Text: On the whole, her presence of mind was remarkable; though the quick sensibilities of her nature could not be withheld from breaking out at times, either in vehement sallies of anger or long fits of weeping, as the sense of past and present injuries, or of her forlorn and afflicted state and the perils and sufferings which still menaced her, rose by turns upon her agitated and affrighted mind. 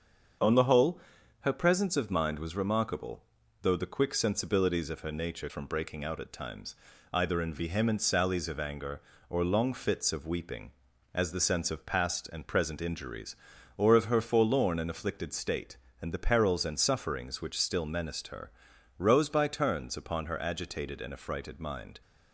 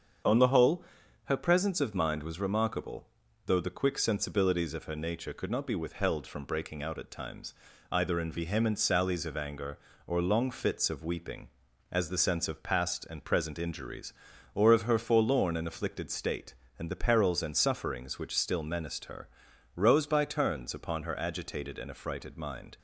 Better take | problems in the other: second | starts louder than the rest; until 1.8 s; 7 dB; strong in the second // skips "could not be withheld"; at 5.4 s

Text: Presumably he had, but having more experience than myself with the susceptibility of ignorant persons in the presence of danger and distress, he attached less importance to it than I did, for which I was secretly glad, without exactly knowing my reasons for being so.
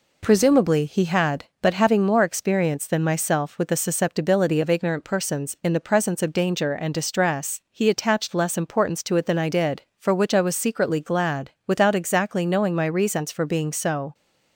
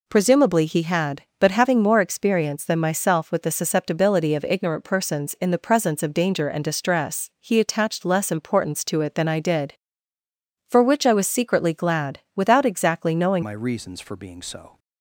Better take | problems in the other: first | changes voice at "my"; from 13.4 s on; 1.3 s long

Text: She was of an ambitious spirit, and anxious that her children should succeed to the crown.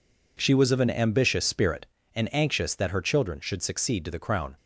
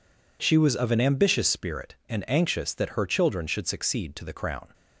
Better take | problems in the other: neither | none

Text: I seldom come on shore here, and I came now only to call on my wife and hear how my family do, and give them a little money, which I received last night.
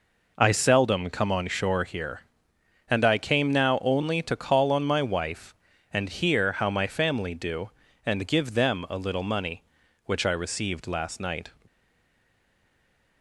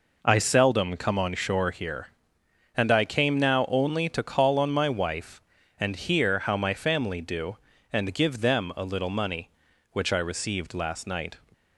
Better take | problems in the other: second | stays silent after the last word; noticeable; from 11.6 s on; 1.6 s long

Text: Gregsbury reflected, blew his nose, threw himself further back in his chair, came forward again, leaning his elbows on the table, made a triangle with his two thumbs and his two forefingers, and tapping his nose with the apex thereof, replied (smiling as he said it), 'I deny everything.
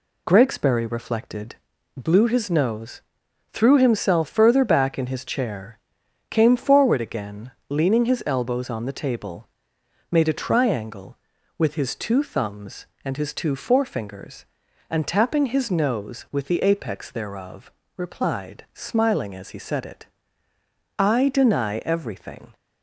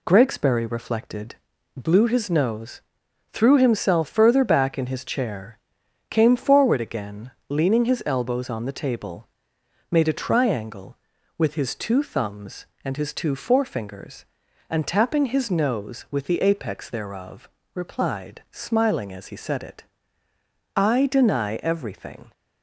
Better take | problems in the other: neither | none

